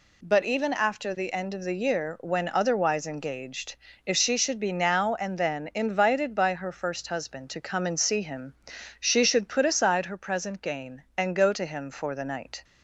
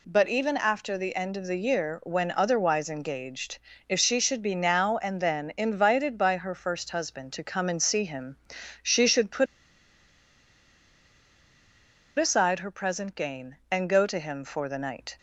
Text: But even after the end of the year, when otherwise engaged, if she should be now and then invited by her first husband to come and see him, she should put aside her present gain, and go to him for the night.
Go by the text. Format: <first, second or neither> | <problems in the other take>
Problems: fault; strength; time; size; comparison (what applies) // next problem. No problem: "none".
first | pauses between "put" and "aside"; strong; at 9.4 s; 2.7 s long